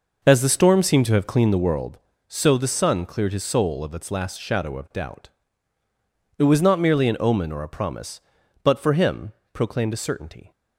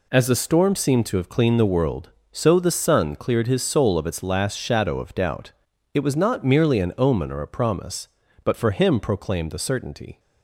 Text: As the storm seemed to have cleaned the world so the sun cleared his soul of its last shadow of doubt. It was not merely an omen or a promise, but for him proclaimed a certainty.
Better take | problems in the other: second | starts louder than the rest; noticeable; until 1.9 s; 5.5 dB // pauses between "him" and "proclaimed"; slight; at 9.3 s; 0.22 s long

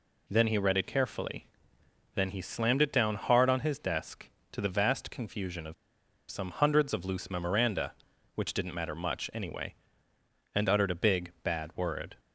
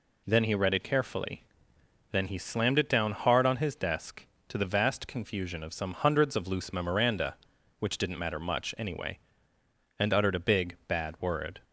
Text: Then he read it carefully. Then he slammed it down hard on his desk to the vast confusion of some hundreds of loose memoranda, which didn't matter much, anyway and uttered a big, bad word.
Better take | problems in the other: second | pauses between "of" and "some"; noticeable; at 5.7 s; 0.56 s long

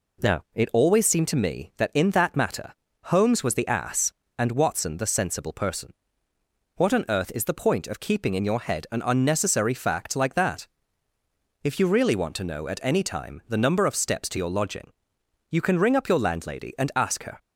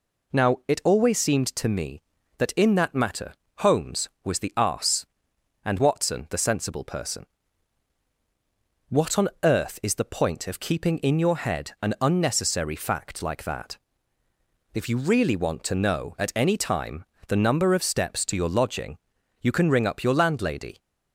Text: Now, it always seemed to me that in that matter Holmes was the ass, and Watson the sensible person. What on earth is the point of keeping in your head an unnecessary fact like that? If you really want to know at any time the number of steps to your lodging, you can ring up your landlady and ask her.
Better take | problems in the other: first | pauses between "matter" and "Holmes"; slight; at 3.3 s; 0.26 s long; slight in the first // pauses between "time" and "the"; slight; at 17.0 s; 0.24 s long // stops before "and ask her"; at 20.7 s

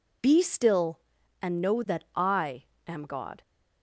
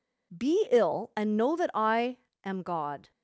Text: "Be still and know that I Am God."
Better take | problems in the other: first | says "ill" for "still"; at 0.6 s // pauses between "I" and "Am"; slight; at 2.1 s; 0.26 s long; slight in the first

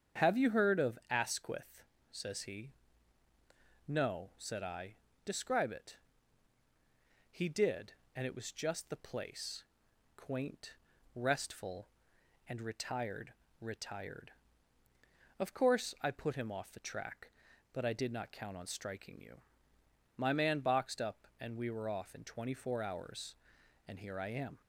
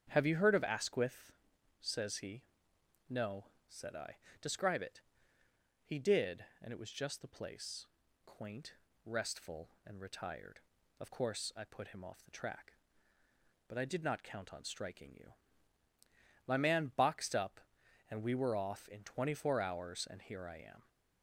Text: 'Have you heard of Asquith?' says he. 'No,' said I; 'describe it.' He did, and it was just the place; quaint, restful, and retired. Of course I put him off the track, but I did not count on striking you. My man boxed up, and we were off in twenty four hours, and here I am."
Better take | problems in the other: second | starts louder than the rest; strong; until 1.3 s; 8 dB; strong in the second // says "retired" twice; at 13.6 s

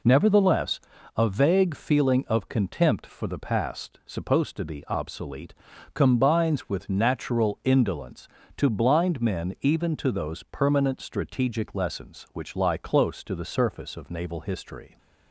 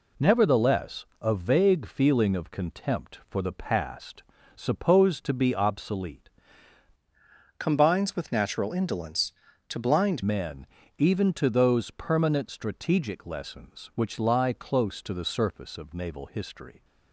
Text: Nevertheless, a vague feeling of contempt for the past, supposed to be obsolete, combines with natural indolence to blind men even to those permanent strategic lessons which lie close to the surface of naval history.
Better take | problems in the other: first | changes voice from "combines" to "blind"; from 7.5 to 10.2 s; 2.7 s long // pauses between "men" and "even"; slight; at 10.6 s; 0.32 s long

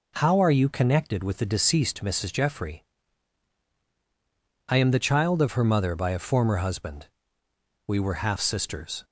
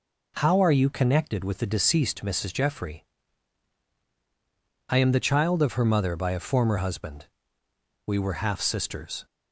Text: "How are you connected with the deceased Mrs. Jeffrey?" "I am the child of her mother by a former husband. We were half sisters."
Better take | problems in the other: neither | none

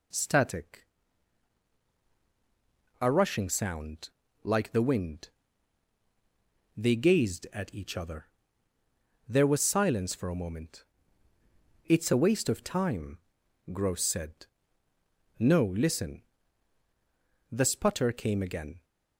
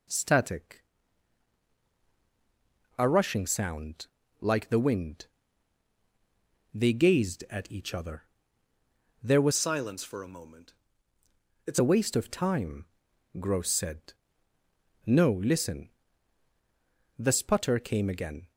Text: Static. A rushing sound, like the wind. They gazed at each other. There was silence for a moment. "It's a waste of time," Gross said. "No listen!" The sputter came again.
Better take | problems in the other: first | changes voice from "silence" to "It's"; from 9.5 to 11.7 s; 2.2 s long

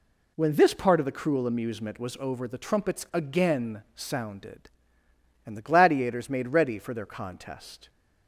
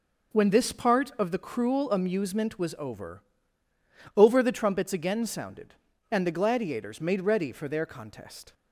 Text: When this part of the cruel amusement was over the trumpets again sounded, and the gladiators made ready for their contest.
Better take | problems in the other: first | says "over" twice; at 4.1 s

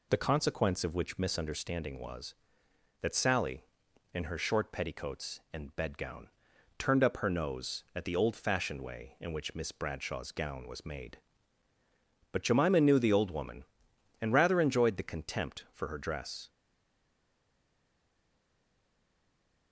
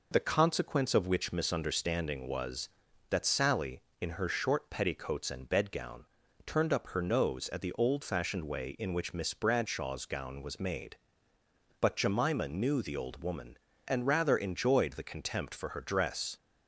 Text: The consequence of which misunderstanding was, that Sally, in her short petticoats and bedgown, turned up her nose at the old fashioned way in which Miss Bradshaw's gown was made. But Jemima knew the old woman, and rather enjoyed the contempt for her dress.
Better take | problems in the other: second | stays silent after the last word; strong; from 16.4 s on; 3.3 s long

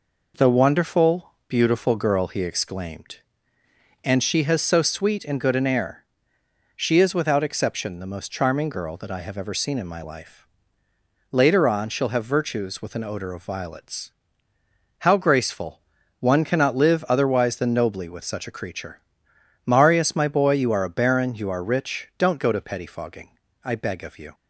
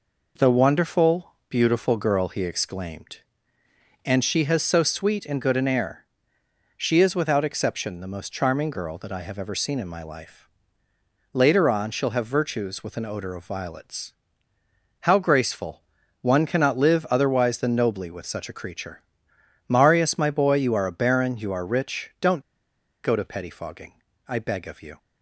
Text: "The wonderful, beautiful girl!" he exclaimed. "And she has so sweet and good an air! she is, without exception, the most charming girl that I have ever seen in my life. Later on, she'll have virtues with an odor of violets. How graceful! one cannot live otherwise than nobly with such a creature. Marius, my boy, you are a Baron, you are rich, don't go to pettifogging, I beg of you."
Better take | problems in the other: first | pauses between "don't" and "go"; noticeable; at 22.4 s; 0.61 s long

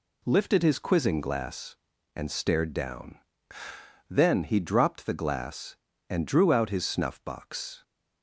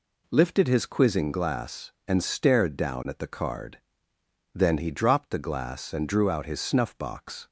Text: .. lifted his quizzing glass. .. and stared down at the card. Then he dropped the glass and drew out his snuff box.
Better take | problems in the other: second | skips "at the card"; at 3.6 s

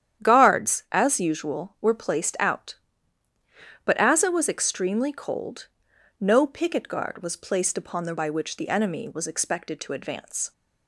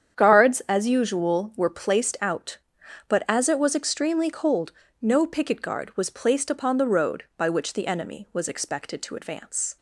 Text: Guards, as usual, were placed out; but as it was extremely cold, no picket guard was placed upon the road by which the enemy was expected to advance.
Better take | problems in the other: second | starts louder than the rest; strong; until 1.3 s; 10 dB; strong in the second // skips "road"; at 8.1 s

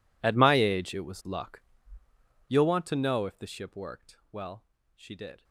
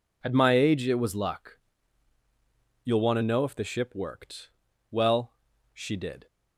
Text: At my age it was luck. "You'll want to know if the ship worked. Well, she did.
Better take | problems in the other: second | gets quieter; strong; throughout; 22 dB

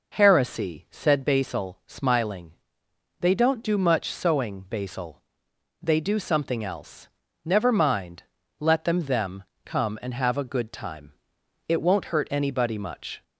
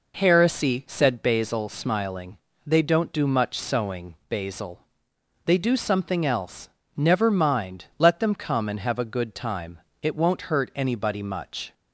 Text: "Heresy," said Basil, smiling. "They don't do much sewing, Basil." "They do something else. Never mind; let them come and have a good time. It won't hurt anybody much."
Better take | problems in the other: second | says "them" twice; at 9.0 s

